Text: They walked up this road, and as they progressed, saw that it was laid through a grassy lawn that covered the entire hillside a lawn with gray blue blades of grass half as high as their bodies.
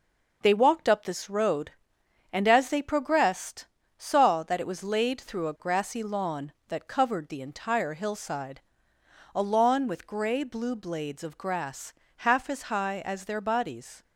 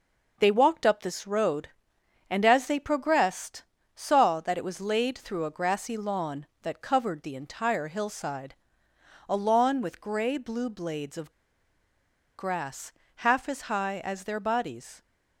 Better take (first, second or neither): first